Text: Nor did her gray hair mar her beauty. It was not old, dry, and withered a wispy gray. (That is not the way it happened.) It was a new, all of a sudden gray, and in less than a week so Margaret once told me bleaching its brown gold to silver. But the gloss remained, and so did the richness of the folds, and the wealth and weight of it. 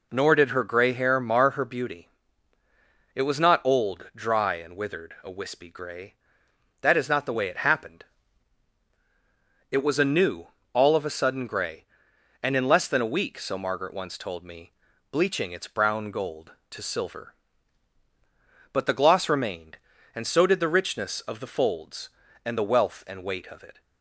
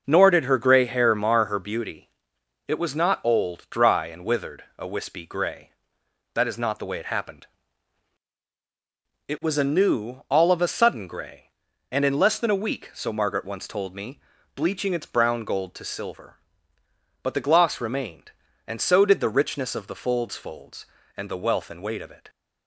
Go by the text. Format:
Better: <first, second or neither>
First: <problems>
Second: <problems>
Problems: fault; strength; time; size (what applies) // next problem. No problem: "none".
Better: first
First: pauses between "me" and "bleaching"; at 14.7 s; 0.38 s long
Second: pauses between "me" and "bleaching"; slight; at 14.2 s; 0.34 s long // says "folds" twice; at 20.3 s